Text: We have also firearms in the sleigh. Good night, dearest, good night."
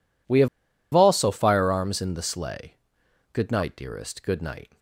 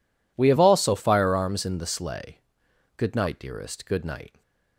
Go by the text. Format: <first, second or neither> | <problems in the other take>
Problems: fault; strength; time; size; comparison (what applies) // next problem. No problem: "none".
second | pauses between "have" and "also"; noticeable; at 0.4 s; 0.46 s long